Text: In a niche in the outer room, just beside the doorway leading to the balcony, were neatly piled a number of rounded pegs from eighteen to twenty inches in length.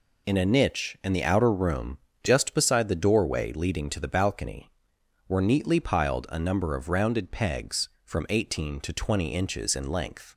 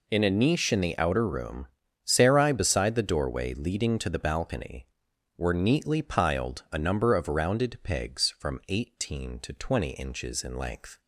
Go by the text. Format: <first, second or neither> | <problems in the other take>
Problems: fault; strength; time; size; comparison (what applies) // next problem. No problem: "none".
first | says "sarai" for "just"; at 2.0 s